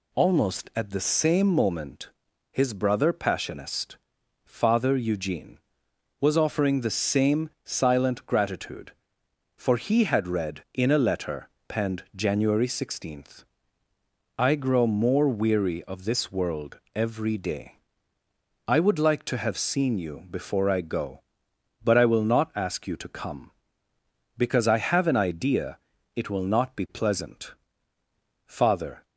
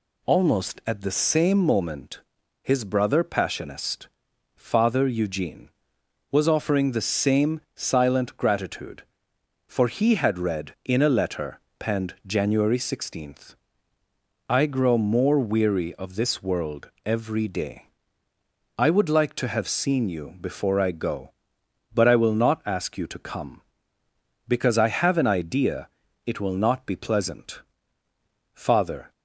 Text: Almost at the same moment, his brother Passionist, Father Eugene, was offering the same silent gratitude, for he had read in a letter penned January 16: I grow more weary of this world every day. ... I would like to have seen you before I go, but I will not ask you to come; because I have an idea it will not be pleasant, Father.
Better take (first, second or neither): neither